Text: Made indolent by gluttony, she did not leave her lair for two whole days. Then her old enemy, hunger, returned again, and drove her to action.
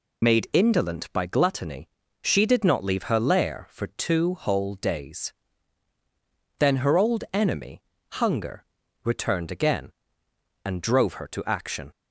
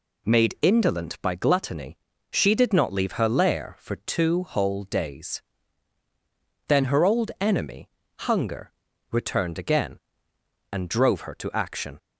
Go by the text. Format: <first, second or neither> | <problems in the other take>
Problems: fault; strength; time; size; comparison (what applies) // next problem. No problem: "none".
second | loses the start of "Made"; at 0.2 s; 45 ms